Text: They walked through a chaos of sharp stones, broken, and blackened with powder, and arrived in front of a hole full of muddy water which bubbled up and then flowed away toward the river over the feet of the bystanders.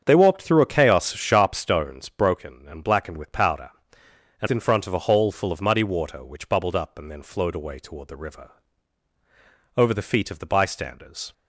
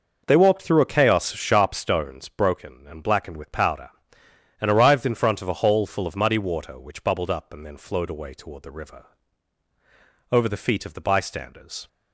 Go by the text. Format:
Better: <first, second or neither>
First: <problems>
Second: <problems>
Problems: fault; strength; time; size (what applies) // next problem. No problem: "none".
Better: second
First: starts louder than the rest; strong; until 1.0 s; 7.5 dB // skips "arrived"; at 4.4 s // pauses between "river" and "over"; strong; at 8.5 s; 1.2 s long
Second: pauses between "river" and "over"; strong; at 9.0 s; 1.2 s long